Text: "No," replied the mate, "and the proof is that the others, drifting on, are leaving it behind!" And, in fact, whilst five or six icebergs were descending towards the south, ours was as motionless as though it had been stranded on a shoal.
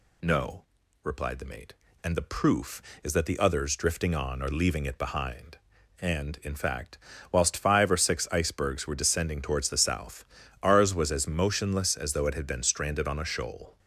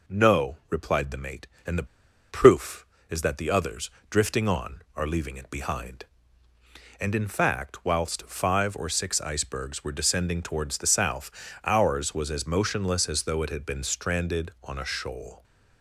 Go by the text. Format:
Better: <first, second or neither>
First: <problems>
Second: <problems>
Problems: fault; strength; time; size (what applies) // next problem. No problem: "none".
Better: first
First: none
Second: pauses between "the" and "proof"; at 1.8 s; 0.45 s long